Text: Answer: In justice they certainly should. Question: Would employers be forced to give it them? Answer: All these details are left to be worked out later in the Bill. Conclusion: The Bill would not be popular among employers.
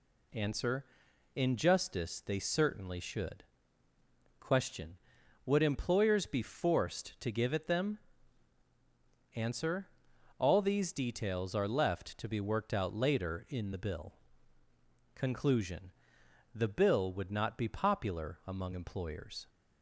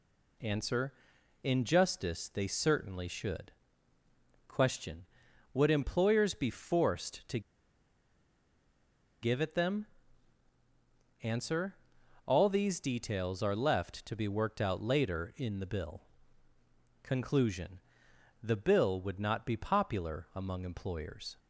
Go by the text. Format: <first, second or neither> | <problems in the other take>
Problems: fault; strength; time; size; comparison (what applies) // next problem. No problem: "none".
first | pauses between "to" and "give"; strong; at 7.3 s; 1.8 s long